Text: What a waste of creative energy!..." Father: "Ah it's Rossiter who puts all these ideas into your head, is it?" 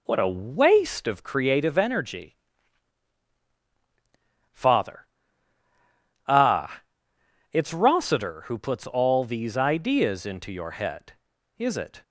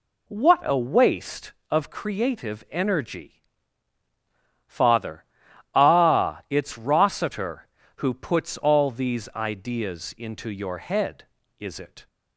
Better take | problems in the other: second | starts louder than the rest; until 1.2 s; 3.5 dB // pauses between "Ah" and "it's"; noticeable; at 6.8 s; 0.68 s long

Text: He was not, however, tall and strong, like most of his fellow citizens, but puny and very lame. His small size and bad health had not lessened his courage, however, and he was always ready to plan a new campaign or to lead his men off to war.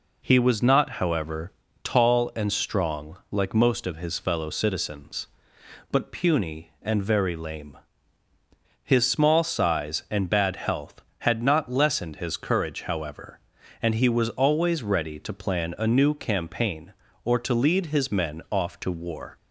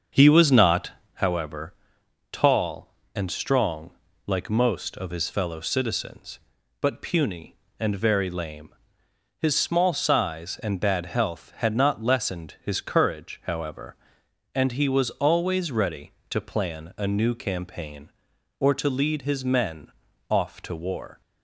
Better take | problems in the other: first | starts louder than the rest; until 1.2 s; 6.5 dB // pauses between "men" and "off"; at 19.9 s; 0.38 s long

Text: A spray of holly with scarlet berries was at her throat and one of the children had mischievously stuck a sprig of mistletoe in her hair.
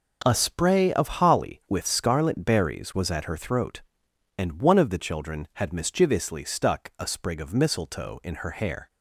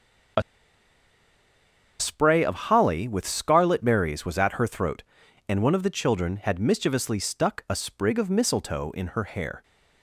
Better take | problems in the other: first | starts louder than the rest; until 2.9 s; 7 dB // pauses between "A" and "spray"; strong; at 0.4 s; 1.5 s long

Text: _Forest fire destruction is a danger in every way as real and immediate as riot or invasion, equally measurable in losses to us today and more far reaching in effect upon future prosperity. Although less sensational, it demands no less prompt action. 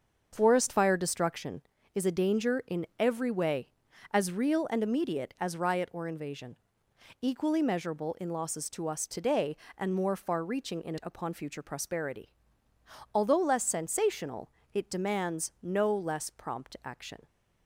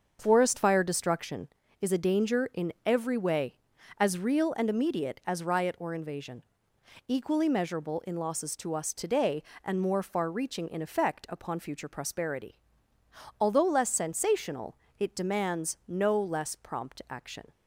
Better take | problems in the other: second | starts louder than the rest; until 1.3 s; 7 dB; also in the second // skips "effect"; at 10.9 s

